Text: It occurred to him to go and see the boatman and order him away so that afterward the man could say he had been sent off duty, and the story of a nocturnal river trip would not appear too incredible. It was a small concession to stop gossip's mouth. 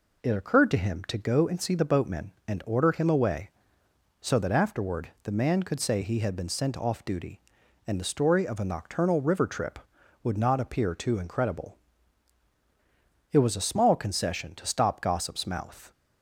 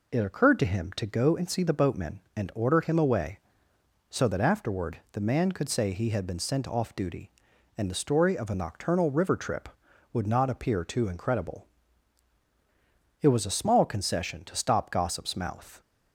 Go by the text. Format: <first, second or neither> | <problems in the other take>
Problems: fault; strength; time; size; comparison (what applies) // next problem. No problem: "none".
neither | none